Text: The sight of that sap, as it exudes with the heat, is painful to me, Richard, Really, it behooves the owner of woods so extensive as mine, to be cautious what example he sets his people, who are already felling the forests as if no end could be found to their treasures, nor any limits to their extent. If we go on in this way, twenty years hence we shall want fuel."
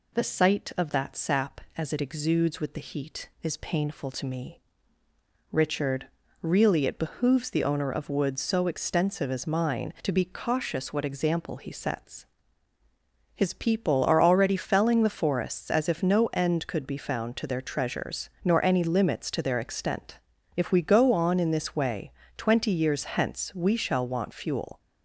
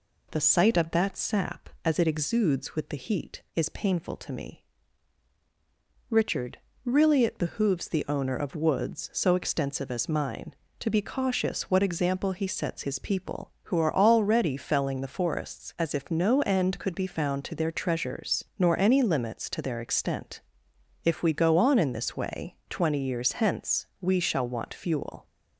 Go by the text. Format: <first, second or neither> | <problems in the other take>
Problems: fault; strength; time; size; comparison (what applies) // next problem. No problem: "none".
second | pauses between "sets" and "his"; at 12.2 s; 1.0 s long // skips "who"; at 14.0 s